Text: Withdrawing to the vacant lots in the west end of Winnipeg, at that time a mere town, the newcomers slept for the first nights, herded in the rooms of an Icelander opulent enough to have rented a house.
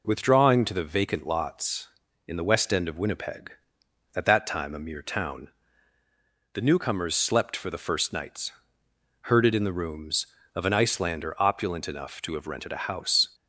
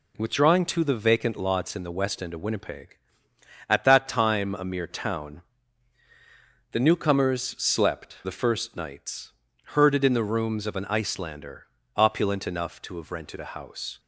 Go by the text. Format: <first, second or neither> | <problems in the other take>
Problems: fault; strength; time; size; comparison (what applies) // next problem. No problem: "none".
first | pauses between "newcomers" and "slept"; slight; at 7.4 s; 0.18 s long // skips "for"; at 8.2 s // pauses between "Icelander" and "opulent"; slight; at 11.6 s; 0.32 s long